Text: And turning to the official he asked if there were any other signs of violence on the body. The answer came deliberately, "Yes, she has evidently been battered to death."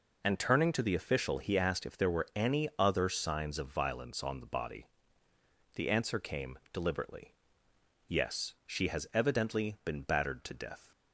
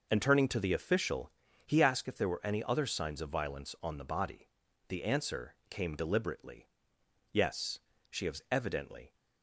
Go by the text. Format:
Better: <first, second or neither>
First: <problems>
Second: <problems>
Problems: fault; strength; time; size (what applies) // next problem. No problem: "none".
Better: first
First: none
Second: pauses between "official" and "he"; slight; at 1.3 s; 0.36 s long // stops before "been battered to death"; at 9.1 s